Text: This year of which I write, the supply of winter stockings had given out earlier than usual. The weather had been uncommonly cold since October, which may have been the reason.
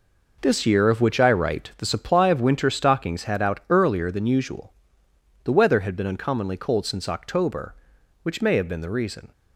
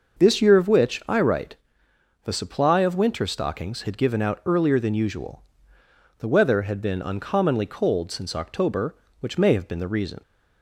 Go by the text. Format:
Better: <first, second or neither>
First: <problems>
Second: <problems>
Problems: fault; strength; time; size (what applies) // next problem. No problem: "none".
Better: second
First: skips "given"; at 3.4 s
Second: none